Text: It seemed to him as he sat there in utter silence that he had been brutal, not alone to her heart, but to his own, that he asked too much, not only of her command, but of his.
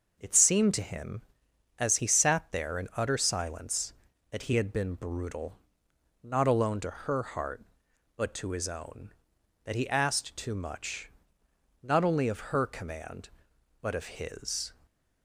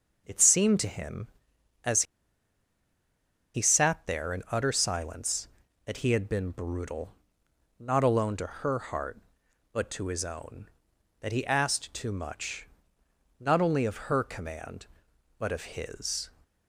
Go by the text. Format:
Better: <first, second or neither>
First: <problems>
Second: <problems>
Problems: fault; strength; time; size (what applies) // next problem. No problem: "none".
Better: first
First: none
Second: pauses between "as" and "he"; strong; at 2.0 s; 1.5 s long